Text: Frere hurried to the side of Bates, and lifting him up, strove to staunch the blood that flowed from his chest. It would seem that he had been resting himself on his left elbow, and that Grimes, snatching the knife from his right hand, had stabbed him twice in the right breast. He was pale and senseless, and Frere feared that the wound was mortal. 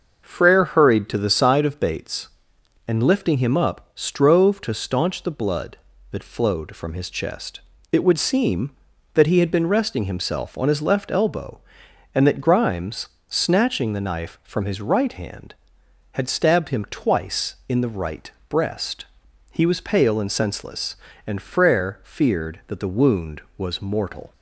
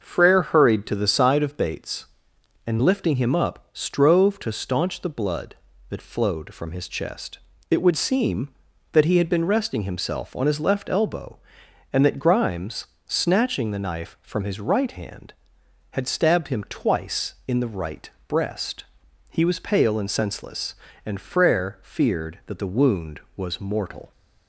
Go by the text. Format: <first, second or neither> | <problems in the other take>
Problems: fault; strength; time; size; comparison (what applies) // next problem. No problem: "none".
neither | starts louder than the rest; noticeable; the same in both // pauses between "right" and "breast"; slight; the same in both